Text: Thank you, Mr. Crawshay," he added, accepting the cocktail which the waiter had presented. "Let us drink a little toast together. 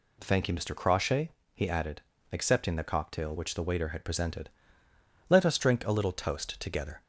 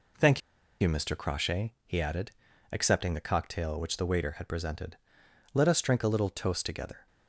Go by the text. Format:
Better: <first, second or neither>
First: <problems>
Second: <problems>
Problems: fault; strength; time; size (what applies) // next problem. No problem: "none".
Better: first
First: none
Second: pauses between "Thank" and "you"; at 0.3 s; 0.40 s long